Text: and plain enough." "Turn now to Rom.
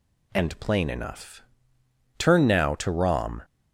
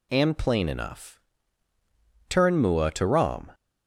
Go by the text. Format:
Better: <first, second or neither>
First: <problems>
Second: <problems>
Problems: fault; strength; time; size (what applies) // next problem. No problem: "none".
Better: first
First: none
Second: says "mua" for "now"; at 2.6 s